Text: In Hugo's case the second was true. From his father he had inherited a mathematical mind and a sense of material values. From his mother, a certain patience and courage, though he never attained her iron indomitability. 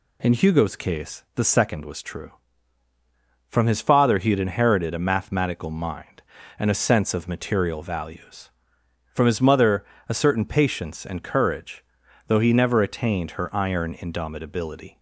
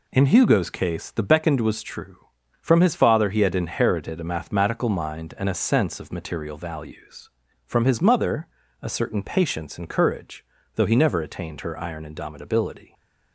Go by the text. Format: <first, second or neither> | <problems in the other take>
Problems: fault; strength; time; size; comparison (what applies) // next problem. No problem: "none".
first | says "beckoned" for "second"; at 1.2 s